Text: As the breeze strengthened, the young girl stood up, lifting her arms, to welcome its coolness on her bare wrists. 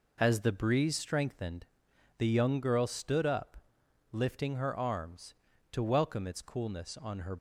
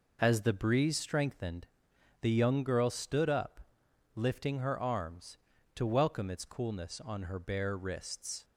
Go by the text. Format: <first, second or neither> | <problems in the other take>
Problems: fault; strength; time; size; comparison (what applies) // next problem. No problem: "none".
second | stops before "bare wrists"; at 7.3 s